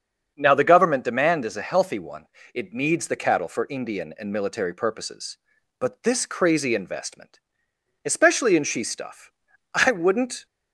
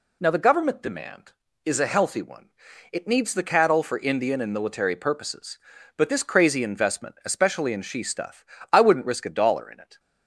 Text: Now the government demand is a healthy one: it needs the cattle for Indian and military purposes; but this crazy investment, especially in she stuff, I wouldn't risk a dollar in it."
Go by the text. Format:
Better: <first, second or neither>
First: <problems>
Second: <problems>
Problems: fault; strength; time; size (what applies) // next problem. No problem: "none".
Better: second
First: starts louder than the rest; until 1.3 s; 7 dB // stops before "risk a dollar in it"; at 10.4 s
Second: none